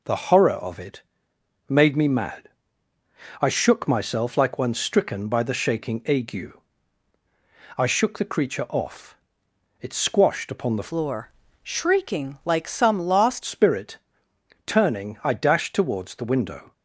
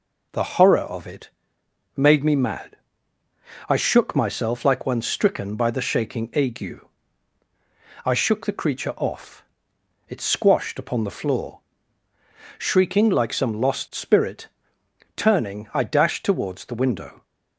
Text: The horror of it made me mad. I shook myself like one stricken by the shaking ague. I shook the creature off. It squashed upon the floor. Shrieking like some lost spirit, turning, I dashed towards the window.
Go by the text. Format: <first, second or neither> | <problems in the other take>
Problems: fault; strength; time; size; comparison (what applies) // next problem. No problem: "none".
second | pauses between "it" and "made"; noticeable; at 1.0 s; 0.68 s long; noticeable in the second // changes voice from "floor" to "lost"; from 10.8 to 13.4 s; 2.6 s long